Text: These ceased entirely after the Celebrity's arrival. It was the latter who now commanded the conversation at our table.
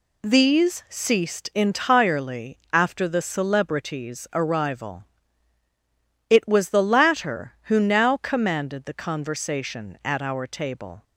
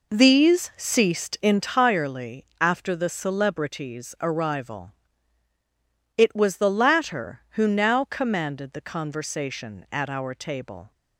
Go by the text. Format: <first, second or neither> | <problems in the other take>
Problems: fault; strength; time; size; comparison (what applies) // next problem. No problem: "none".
first | starts louder than the rest; noticeable; until 1.7 s; 4 dB // pauses between "entirely" and "after"; slight; at 2.4 s; 0.16 s long; slight in the first